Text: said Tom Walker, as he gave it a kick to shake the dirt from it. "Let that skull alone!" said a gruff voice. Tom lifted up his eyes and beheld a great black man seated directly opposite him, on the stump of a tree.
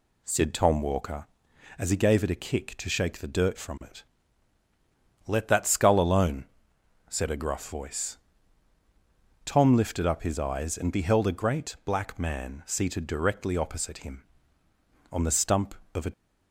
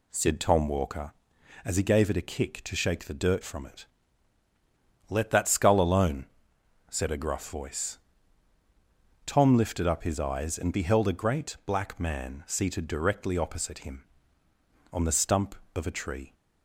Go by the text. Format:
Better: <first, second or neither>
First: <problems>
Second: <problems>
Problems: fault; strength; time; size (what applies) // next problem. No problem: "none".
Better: second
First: stops before "tree"; at 16.1 s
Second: none